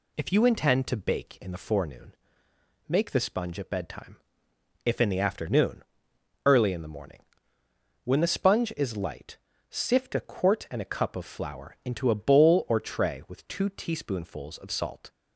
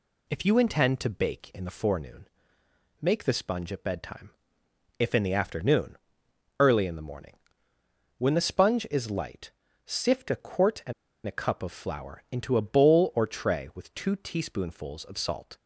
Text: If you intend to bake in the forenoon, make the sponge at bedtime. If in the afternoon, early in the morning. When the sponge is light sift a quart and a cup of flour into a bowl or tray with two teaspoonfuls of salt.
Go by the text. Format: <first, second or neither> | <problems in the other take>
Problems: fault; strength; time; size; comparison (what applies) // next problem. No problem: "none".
first | pauses between "light" and "sift"; slight; at 9.5 s; 0.34 s long; slight in the first // pauses between "and" and "a"; slight; at 10.9 s; 0.33 s long